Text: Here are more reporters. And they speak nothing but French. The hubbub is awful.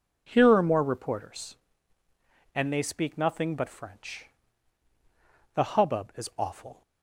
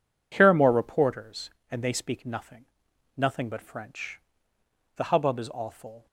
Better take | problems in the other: first | says "nothing" twice; at 3.1 s

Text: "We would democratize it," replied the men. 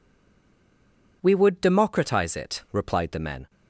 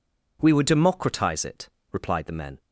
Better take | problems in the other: second | stays silent before the first word; noticeable; until 1.2 s; 1.2 s long

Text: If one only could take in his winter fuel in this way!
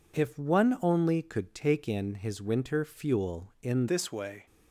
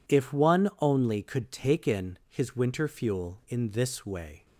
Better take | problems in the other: second | changes voice at "this"; from 3.8 s on; 0.6 s long

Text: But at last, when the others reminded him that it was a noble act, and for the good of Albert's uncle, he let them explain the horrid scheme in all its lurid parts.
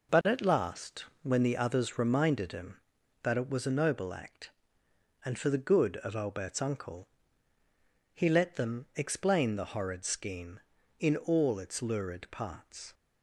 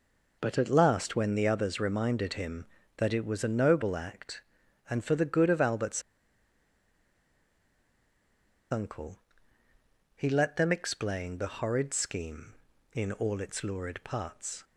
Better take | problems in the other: first | pauses between "Albert's" and "uncle"; strong; at 6.0 s; 2.6 s long

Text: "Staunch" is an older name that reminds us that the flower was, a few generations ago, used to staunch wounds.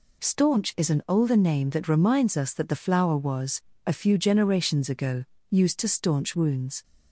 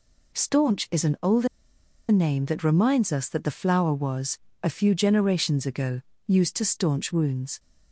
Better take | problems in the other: first | pauses between "older" and "name"; noticeable; at 1.4 s; 0.63 s long

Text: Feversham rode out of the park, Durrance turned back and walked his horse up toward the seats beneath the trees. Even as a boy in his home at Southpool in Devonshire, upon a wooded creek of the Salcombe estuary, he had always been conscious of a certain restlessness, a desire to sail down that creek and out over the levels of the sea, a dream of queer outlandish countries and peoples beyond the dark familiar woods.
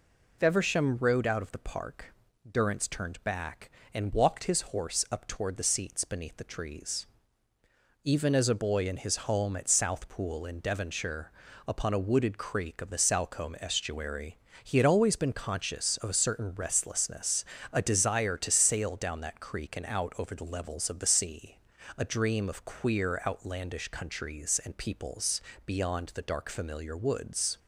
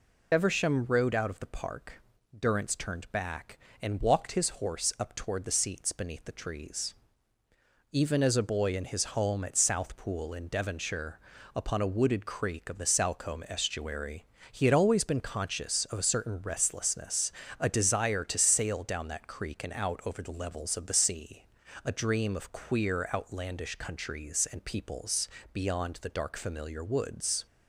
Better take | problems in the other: first | loses the start of "Feversham"; at 0.3 s; 45 ms // pauses between "peoples" and "beyond"; slight; at 25.2 s; 0.26 s long; slight in the first

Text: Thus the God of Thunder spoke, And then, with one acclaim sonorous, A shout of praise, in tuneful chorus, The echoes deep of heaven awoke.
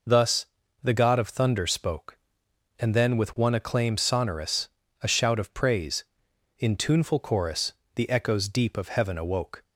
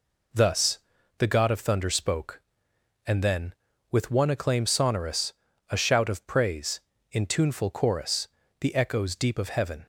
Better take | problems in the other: first | pauses between "Thus" and "the"; at 0.7 s; 0.38 s long; slight in the first // stops before "awoke"; at 9.8 s

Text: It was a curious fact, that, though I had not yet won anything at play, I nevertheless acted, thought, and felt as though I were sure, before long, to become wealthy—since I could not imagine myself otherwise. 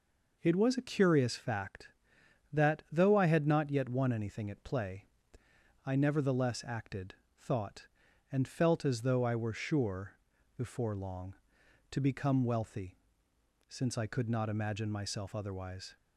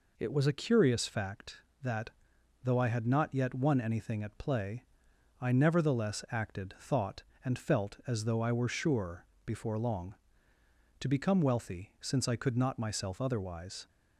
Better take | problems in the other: first | skips "imagine"; at 12.7 s

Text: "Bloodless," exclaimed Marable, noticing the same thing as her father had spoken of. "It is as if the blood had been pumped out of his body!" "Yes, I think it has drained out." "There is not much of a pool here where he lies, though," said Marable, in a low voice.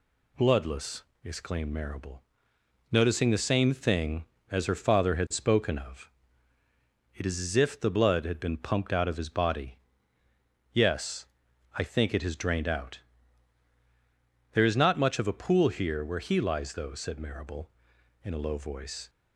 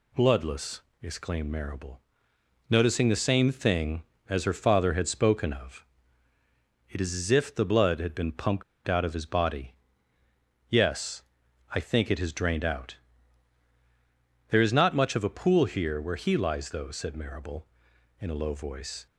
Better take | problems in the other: first | pauses between "pumped" and "out"; slight; at 8.6 s; 0.24 s long

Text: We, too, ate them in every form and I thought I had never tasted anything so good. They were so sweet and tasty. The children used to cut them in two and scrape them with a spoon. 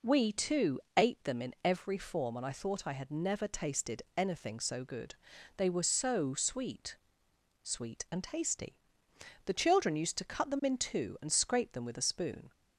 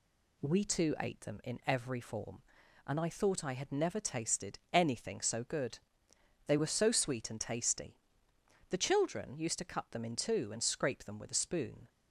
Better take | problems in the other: second | says "sweet" twice; at 7.6 s

